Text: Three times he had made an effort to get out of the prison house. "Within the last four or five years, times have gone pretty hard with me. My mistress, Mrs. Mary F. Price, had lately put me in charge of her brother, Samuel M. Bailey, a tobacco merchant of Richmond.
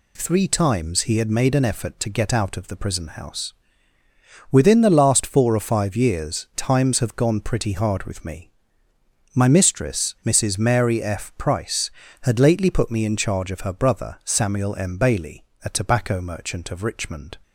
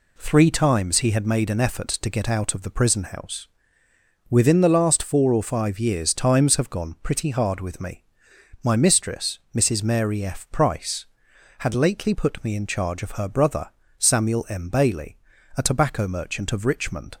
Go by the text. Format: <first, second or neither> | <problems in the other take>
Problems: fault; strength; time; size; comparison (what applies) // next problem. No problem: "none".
neither | none